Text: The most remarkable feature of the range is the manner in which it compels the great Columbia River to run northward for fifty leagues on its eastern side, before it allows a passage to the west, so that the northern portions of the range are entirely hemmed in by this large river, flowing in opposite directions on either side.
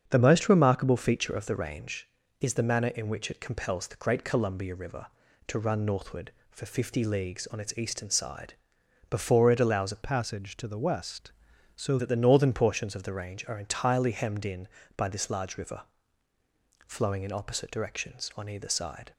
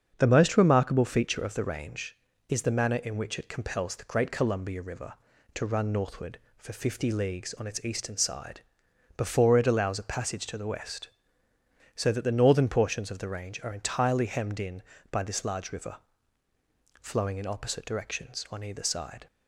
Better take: second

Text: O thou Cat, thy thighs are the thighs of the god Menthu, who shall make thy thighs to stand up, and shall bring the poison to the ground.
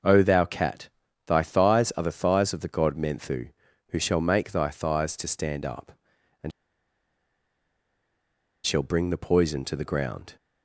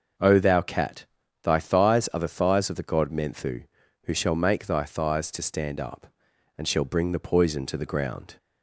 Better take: second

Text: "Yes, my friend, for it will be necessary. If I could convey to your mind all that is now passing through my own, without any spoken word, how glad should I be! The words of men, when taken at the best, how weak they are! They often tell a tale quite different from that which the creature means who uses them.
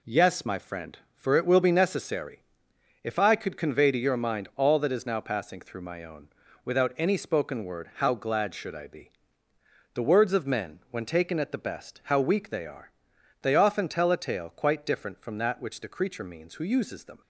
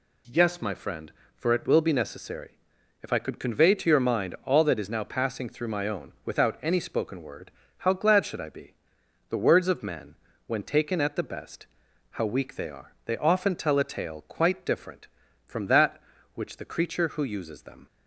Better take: first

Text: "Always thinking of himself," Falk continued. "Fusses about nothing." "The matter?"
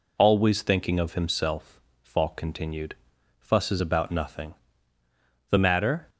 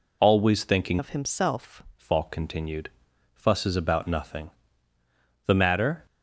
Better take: first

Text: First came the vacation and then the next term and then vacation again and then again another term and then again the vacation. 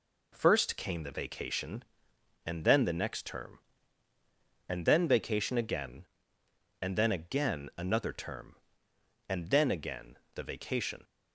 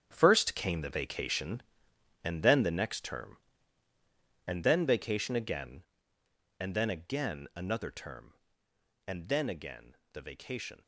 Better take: first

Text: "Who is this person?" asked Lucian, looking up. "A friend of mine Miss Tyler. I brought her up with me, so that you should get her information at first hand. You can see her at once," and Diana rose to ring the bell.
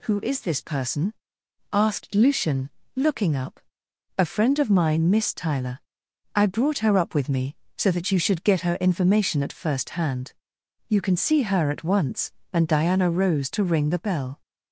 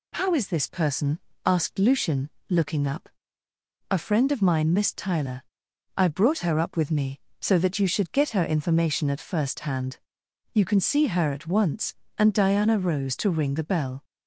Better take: first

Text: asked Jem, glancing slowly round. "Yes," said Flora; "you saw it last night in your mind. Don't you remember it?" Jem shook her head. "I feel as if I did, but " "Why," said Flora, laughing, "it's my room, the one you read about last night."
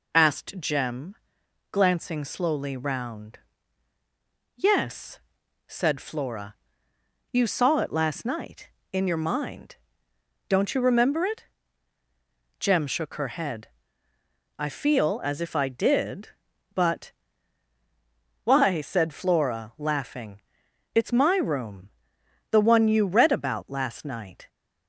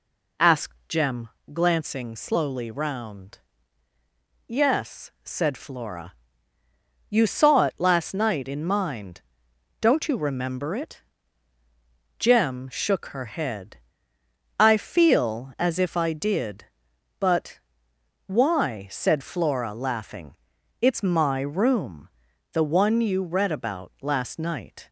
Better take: first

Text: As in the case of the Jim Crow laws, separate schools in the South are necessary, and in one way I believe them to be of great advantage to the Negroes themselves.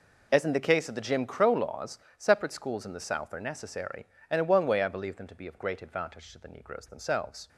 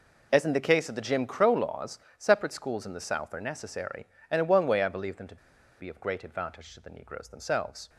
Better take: first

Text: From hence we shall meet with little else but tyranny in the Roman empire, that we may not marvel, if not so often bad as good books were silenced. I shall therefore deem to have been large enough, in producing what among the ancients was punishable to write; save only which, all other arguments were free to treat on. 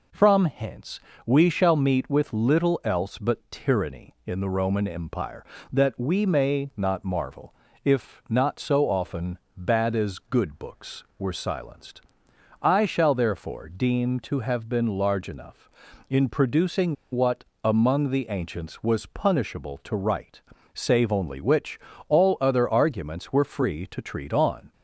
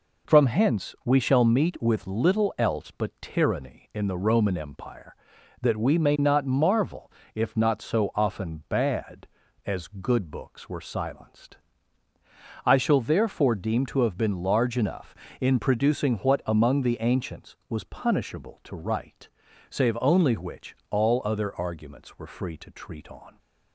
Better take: second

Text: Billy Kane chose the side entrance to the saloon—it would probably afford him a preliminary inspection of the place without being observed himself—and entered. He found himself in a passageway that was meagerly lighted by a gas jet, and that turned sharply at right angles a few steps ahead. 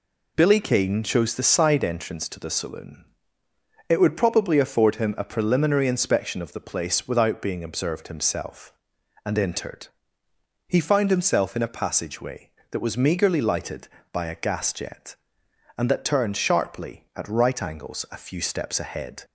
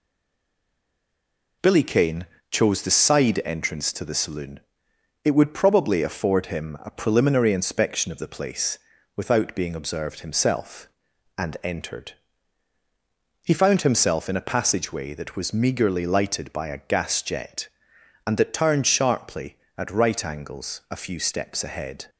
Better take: first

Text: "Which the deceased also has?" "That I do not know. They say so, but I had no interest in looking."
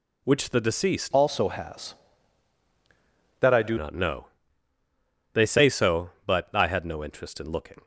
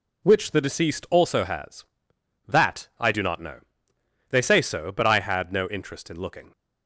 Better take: second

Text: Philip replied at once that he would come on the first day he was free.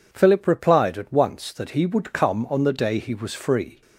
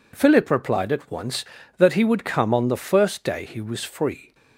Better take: second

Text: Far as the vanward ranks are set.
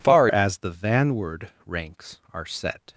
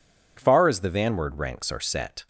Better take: second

